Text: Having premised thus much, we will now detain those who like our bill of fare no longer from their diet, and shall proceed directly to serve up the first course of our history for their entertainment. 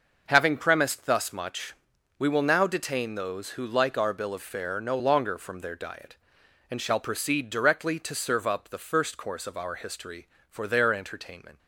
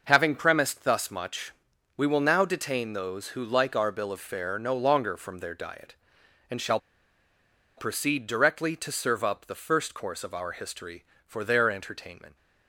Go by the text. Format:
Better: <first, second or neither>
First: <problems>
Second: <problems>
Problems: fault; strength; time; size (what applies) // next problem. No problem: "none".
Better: first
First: none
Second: pauses between "shall" and "proceed"; at 6.7 s; 0.99 s long